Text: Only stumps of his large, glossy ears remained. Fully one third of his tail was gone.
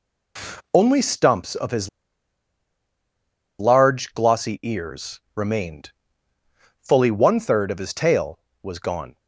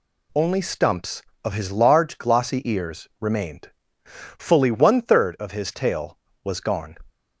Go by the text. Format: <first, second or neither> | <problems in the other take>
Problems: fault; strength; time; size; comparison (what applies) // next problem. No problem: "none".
second | pauses between "his" and "large"; strong; at 1.8 s; 1.7 s long // pauses between "ears" and "remained"; slight; at 5.1 s; 0.16 s long